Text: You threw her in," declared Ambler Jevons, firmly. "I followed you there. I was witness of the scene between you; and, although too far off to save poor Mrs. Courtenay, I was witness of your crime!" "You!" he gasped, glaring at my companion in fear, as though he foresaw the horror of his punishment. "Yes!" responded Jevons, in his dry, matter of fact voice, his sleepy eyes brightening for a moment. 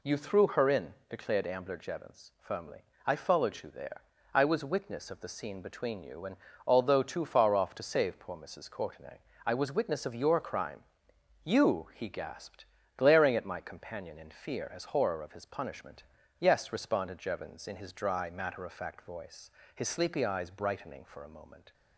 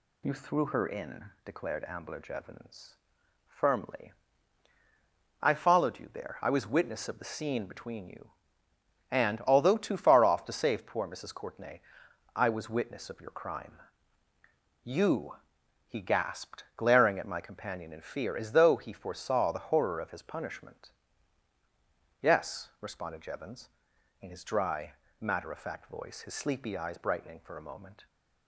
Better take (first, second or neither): second